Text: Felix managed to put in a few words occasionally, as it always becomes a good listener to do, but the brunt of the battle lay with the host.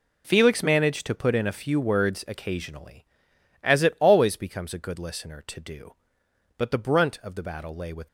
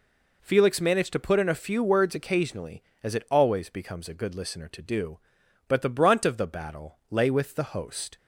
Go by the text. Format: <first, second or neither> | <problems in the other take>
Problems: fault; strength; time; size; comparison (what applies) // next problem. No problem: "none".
second | stops before "the host"; at 8.0 s